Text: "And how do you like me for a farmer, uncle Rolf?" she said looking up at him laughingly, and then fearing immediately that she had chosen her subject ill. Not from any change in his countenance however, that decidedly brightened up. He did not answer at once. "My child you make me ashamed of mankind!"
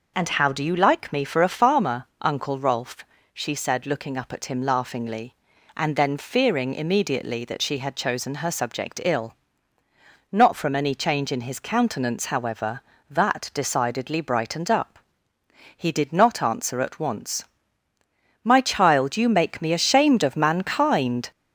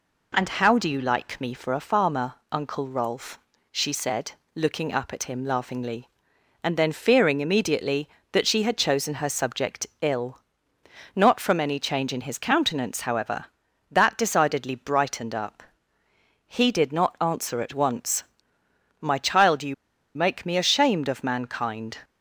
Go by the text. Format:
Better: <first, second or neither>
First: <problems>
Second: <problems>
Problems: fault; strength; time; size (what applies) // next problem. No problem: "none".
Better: first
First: none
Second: pauses between "said" and "looking"; slight; at 4.3 s; 0.24 s long // pauses between "subject" and "ill"; slight; at 9.8 s; 0.16 s long // pauses between "you" and "make"; at 19.7 s; 0.41 s long